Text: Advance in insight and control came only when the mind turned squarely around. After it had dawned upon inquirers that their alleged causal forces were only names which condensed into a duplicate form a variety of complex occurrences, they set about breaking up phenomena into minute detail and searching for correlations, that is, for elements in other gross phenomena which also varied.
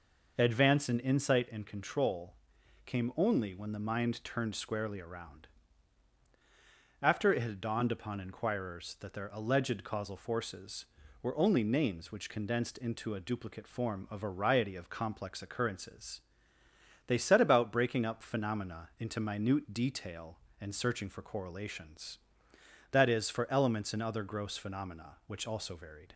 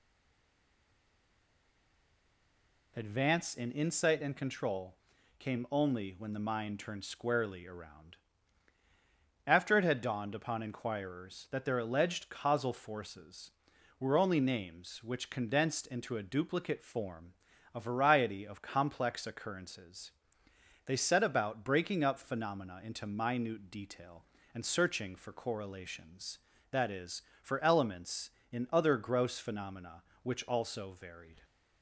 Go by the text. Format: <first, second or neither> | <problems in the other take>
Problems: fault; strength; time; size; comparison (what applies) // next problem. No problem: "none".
first | stays silent before the first word; strong; until 2.9 s; 2.9 s long // pauses between "control" and "came"; at 4.9 s; 0.44 s long; noticeable in the first // pauses between "form" and "a"; at 17.3 s; 0.42 s long